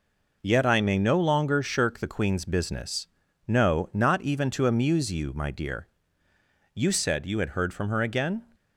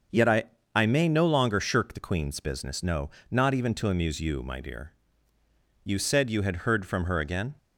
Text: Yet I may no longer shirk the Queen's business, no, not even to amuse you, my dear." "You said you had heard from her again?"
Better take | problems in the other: first | starts louder than the rest; until 1.4 s; 6.5 dB // says "I" twice; at 0.7 s

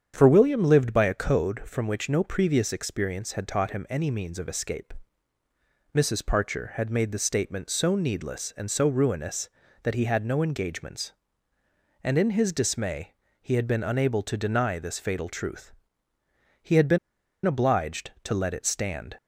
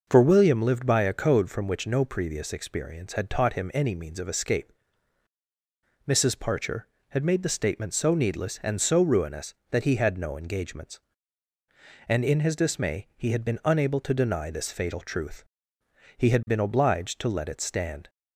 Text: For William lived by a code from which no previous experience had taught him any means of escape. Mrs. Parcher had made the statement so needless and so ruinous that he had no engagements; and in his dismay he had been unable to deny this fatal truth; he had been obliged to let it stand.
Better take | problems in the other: second | starts louder than the rest; strong; until 1.1 s; 8 dB // pauses between "dismay" and "he"; slight; at 13.1 s; 0.30 s long // pauses between "been" and "obliged"; noticeable; at 16.9 s; 0.47 s long

